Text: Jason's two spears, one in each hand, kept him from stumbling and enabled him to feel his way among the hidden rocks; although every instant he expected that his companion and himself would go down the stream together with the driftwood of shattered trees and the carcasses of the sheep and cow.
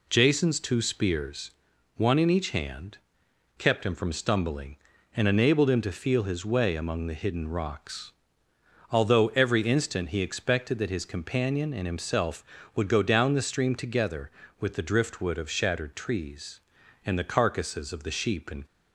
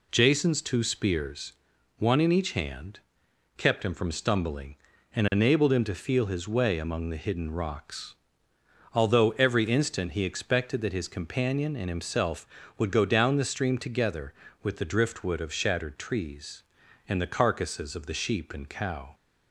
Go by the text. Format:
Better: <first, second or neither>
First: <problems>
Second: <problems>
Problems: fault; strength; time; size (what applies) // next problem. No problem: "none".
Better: second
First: stops before "cow"; at 18.6 s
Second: none